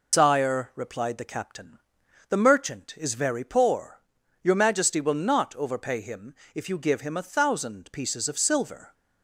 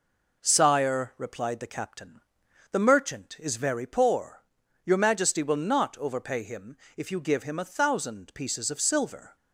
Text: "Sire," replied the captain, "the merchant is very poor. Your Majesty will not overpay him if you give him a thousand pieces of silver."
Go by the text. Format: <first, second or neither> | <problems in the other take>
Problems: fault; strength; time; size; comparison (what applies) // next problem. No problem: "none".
second | loses the start of "Sire"; at 0.1 s; 135 ms // pauses between "him" and "if"; slight; at 6.3 s; 0.20 s long; slight in the second